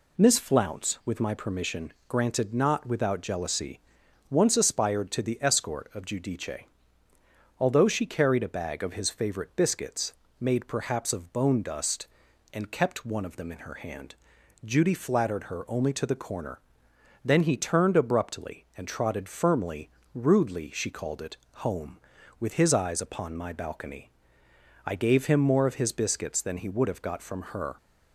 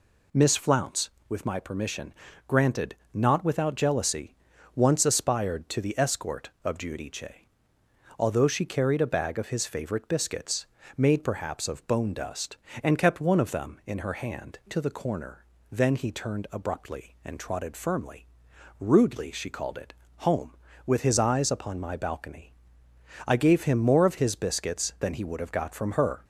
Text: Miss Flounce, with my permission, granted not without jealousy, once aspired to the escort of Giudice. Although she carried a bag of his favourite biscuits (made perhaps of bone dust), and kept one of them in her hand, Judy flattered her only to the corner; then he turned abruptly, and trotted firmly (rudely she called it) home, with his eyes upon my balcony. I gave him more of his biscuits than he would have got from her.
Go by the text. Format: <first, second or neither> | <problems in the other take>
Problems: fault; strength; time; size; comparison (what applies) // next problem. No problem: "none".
first | pauses between "granted" and "not"; slight; at 2.9 s; 0.18 s long // skips "Judy flattered her only"; at 14.6 s